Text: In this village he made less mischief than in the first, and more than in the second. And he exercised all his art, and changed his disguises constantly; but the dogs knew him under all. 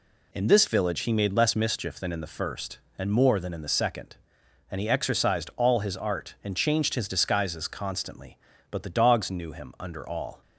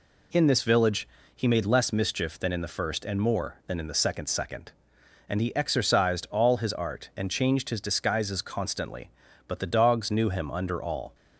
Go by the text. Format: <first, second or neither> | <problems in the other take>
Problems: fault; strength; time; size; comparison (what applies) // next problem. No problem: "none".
first | pauses between "village" and "he"; slight; at 1.0 s; 0.26 s long // says "second" twice; at 4.2 s